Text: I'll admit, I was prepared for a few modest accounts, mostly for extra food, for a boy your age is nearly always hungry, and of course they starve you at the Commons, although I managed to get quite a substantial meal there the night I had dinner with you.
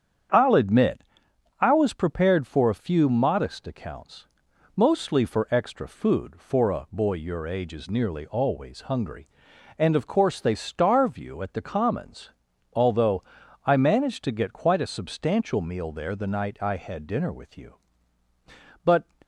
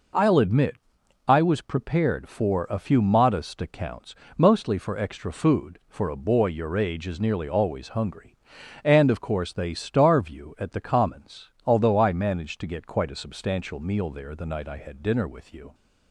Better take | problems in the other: second | starts louder than the rest; strong; until 1.9 s; 8.5 dB // pauses between "although" and "I"; at 13.2 s; 0.42 s long // goes on to say "But"; slight; from 18.8 s on; 0.20 s long

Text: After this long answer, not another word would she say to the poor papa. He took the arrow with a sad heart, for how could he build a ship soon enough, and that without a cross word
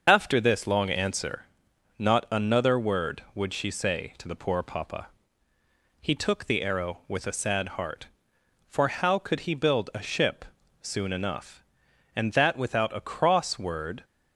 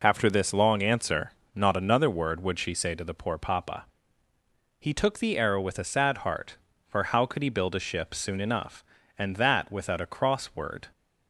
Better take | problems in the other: second | loses the start of "After"; at 0.0 s; 25 ms // starts louder than the rest; until 1.0 s; 6.5 dB // pauses between "ship" and "soon"; slight; at 10.4 s; 0.36 s long

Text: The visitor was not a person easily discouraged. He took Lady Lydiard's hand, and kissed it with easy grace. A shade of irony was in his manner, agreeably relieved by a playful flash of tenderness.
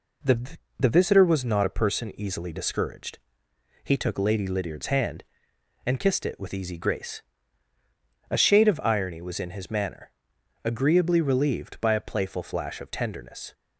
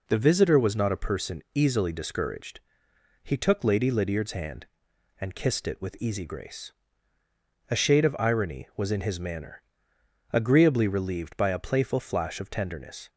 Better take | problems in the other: second | says "The" twice; at 0.7 s

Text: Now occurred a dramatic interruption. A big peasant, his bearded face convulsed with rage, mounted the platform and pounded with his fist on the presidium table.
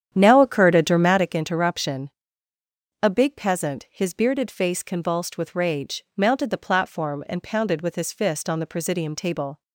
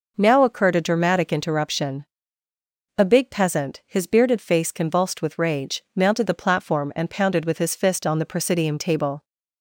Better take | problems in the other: second | starts louder than the rest; strong; until 1.2 s; 9 dB

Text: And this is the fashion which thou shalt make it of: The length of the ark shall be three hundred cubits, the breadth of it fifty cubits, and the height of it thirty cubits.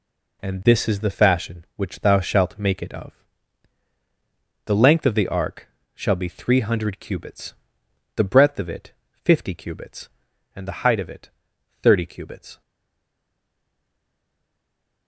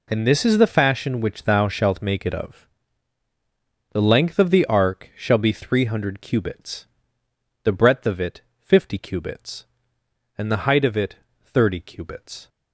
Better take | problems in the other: second | pauses between "ark" and "shall"; slight; at 5.6 s; 0.26 s long // pauses between "it" and "fifty"; slight; at 8.9 s; 0.32 s long; slight in the second // pauses between "it" and "thirty"; noticeable; at 11.2 s; 0.54 s long; slight in the second // stays silent after the last word; from 12.6 s on; 2.4 s long

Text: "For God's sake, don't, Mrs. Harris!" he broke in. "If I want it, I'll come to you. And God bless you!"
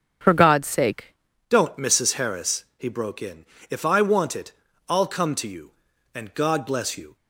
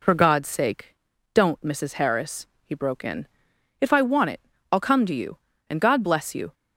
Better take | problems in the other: second | starts louder than the rest; until 1.5 s; 7 dB // changes voice at "don't"; from 1.5 s on; 5.6 s long

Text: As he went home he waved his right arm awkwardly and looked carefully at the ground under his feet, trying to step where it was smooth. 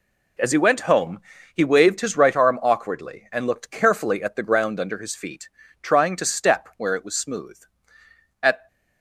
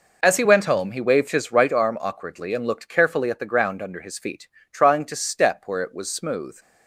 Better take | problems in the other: second | pauses between "home" and "he"; slight; at 1.1 s; 0.35 s long // goes on to say "At"; slight; from 8.4 s on; 0.24 s long

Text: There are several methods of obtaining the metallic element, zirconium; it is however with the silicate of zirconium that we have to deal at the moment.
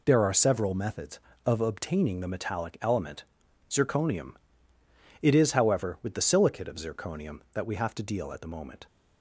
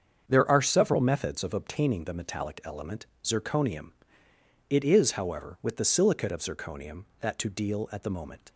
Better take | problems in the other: first | starts louder than the rest; until 1.3 s; 7 dB // skips "we have"; at 7.3 s

